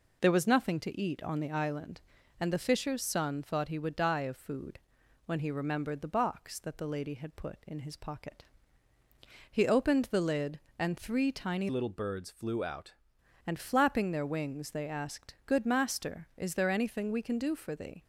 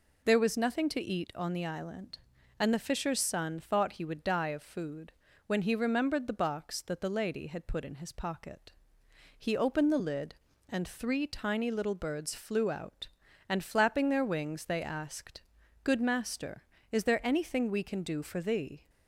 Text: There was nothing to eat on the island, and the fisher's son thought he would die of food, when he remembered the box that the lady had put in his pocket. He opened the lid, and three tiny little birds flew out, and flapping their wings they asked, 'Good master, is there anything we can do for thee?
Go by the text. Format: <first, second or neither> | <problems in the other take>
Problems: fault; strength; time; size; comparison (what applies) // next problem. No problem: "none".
second | changes voice from "little" to "out"; from 11.6 to 12.9 s; 1.3 s long